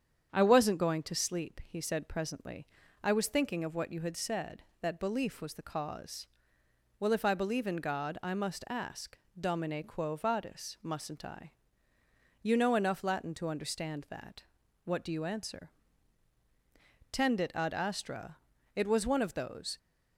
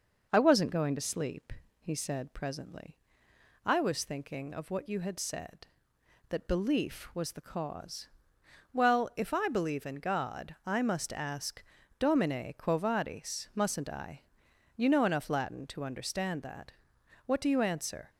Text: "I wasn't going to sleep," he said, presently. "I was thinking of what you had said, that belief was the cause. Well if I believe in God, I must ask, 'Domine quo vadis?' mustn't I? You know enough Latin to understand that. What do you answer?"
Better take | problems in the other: second | starts louder than the rest; strong; until 1.3 s; 8 dB // goes on to say "Tendit ad astra It was one of those"; strong; from 17.1 s on; 2.6 s long

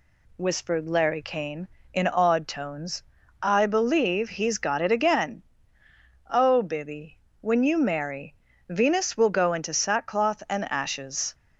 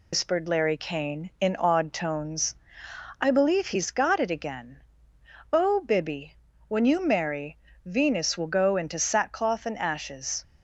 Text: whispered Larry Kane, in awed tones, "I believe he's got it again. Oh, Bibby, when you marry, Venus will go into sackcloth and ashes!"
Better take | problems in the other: first | loses the start of "whispered"; at 0.1 s; 110 ms

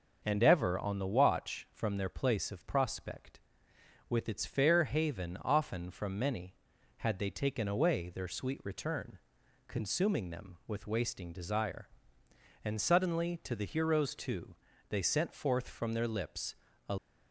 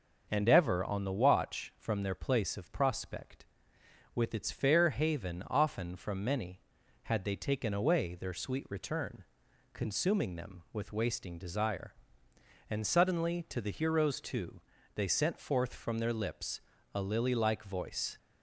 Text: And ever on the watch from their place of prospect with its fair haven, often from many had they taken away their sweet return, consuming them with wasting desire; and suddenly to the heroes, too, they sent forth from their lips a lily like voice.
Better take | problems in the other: second | pauses between "lips" and "a"; slight; at 16.5 s; 0.34 s long; slight in the second // stops before "lily like voice"; at 16.9 s

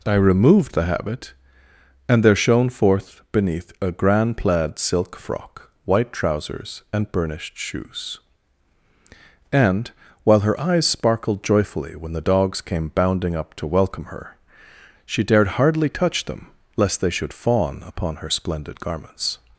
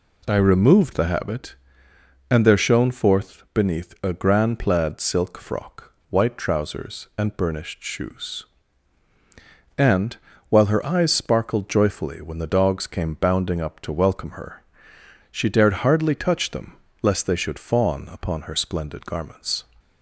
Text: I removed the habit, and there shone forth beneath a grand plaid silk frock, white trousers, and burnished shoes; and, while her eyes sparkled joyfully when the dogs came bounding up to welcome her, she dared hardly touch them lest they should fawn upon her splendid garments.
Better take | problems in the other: neither | pauses between "them" and "lest"; slight; the same in both

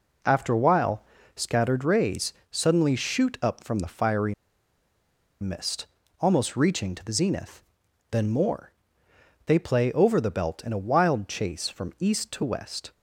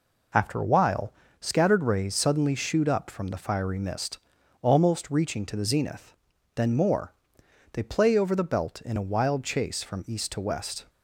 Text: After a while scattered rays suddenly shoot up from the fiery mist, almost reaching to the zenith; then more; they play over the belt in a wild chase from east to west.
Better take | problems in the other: second | pauses between "while" and "scattered"; slight; at 1.0 s; 0.30 s long; slight in the second // pauses between "rays" and "suddenly"; slight; at 2.3 s; 0.16 s long // pauses between "fiery" and "mist"; at 4.3 s; 1.0 s long

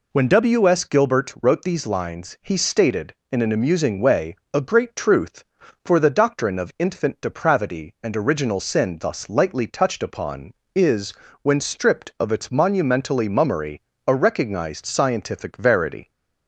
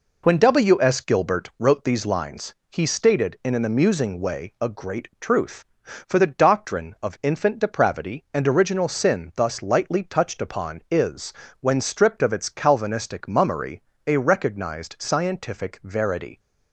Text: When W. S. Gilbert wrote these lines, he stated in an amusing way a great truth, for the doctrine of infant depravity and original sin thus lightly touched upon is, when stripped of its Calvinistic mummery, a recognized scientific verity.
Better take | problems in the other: second | pauses between "way" and "a"; slight; at 4.3 s; 0.18 s long // says "Monumentally" for "Calvinistic"; at 12.4 s

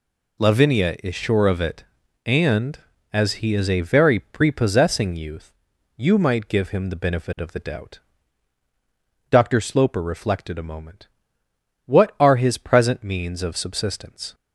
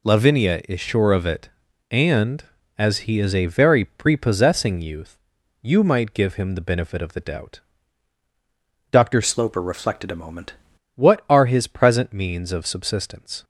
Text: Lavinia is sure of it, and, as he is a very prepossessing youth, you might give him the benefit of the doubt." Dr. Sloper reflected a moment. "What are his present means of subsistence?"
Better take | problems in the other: first | changes voice from "Sloper" to "moment"; from 9.2 to 10.5 s; 1.3 s long

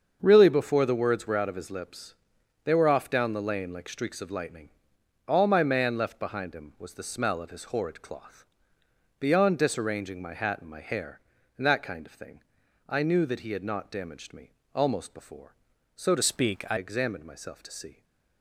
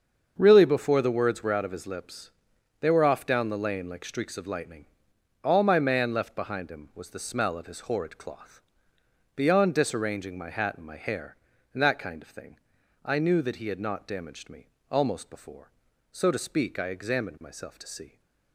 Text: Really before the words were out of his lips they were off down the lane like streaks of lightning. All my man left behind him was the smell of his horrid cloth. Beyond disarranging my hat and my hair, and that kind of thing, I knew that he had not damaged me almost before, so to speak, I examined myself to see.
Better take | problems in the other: second | starts louder than the rest; until 1.2 s; 6.5 dB; also in the second // pauses between "lips" and "they"; noticeable; at 2.1 s; 0.50 s long; noticeable in the second // pauses between "me" and "almost"; slight; at 14.5 s; 0.24 s long; slight in the second // changes voice from "speak" to "I"; from 16.2 to 16.7 s; 0.5 s long

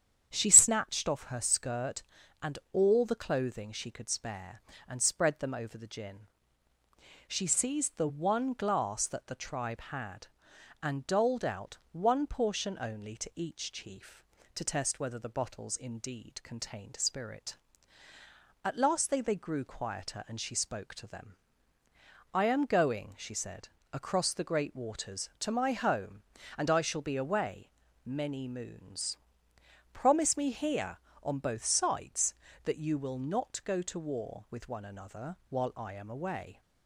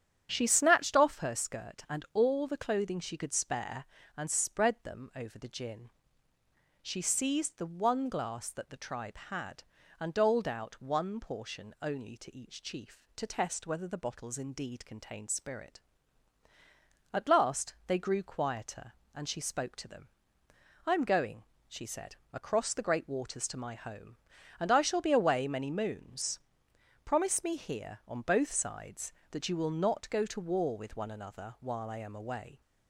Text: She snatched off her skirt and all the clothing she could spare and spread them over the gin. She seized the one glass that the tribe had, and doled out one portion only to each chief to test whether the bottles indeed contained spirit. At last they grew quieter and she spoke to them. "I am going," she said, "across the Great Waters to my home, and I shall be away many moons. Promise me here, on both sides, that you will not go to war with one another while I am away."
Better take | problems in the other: second | starts louder than the rest; strong; until 1.3 s; 9 dB; strong in the second // pauses between "out" and "one"; slight; at 11.7 s; 0.16 s long // says "they" twice; at 19.1 s // pauses between "away" and "many"; slight; at 27.6 s; 0.36 s long

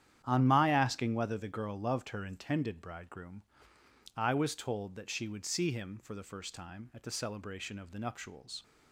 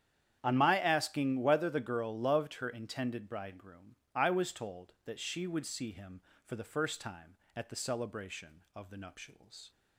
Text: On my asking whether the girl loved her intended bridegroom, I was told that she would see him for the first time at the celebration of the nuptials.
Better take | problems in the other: neither | starts louder than the rest; strong; the same in both

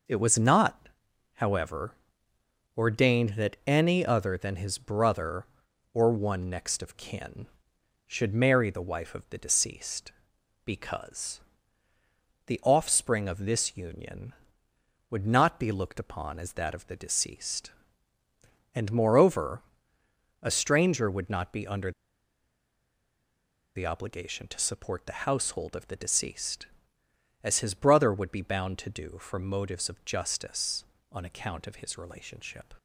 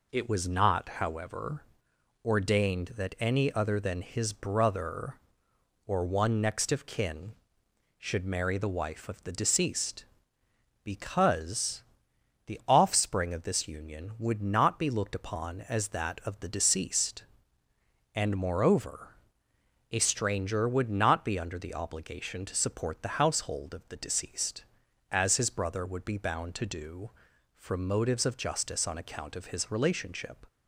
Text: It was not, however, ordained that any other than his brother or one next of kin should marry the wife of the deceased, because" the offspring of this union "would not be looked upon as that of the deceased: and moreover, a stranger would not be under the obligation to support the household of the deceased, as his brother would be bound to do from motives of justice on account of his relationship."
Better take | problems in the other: second | pauses between "because" and "the"; at 11.4 s; 1.0 s long; noticeable in the second // pauses between "under" and "the"; strong; at 21.9 s; 1.8 s long

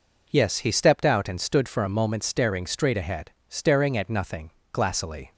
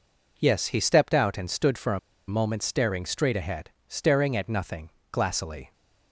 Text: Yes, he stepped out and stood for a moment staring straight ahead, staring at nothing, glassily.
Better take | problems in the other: first | pauses between "a" and "moment"; slight; at 1.9 s; 0.28 s long

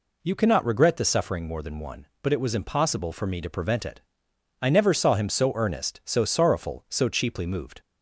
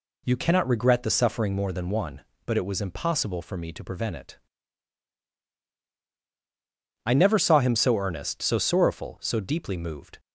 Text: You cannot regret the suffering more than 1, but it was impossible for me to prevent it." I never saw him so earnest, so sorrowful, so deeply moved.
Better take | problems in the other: second | says "cheaply" for "deeply"; at 7.0 s

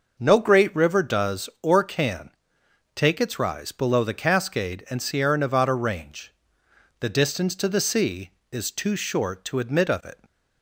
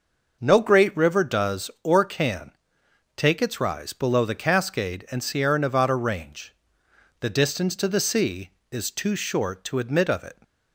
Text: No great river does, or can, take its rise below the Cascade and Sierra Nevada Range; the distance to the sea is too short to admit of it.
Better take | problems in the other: neither | none

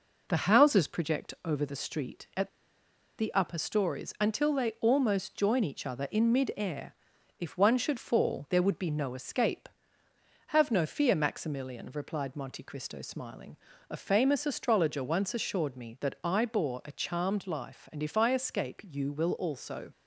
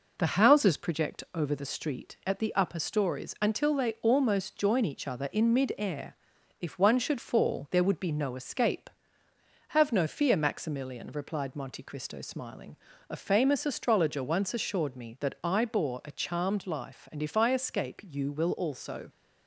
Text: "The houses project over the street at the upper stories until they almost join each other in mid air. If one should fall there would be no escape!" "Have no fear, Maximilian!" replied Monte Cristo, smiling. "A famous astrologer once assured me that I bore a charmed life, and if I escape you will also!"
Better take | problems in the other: second | pauses between "at" and "the"; noticeable; at 2.4 s; 0.69 s long

